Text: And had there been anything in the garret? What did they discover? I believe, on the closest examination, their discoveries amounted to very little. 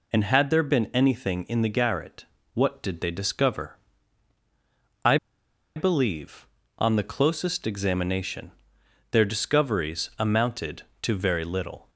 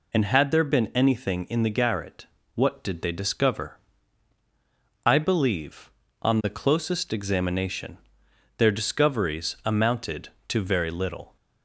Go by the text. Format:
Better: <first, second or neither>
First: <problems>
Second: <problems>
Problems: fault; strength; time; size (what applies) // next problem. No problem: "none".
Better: second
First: pauses between "I" and "believe"; noticeable; at 5.1 s; 0.59 s long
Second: none